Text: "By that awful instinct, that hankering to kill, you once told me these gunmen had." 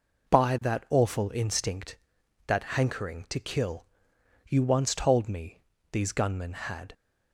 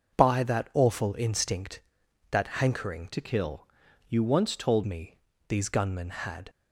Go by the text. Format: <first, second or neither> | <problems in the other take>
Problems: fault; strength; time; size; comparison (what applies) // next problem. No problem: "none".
first | starts louder than the rest; until 1.2 s; 6.5 dB // changes voice from "to" to "told"; from 3.1 to 4.8 s; 1.7 s long // pauses between "me" and "these"; slight; at 5.1 s; 0.28 s long; slight in the first